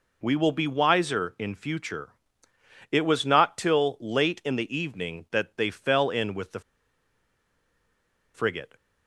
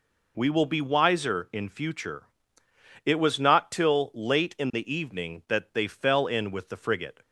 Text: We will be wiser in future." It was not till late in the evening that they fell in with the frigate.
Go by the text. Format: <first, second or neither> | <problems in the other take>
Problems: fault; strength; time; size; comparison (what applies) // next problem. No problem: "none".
second | pauses between "the" and "frigate"; strong; at 6.5 s; 1.7 s long